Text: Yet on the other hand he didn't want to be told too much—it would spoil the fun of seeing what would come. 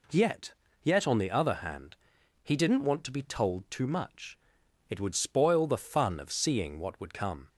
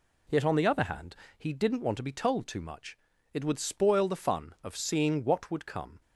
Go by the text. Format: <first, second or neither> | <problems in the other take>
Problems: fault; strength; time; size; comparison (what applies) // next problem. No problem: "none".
second | says "Yet" twice; at 0.8 s // pauses between "hand" and "he"; noticeable; at 1.9 s; 0.48 s long; slight in the second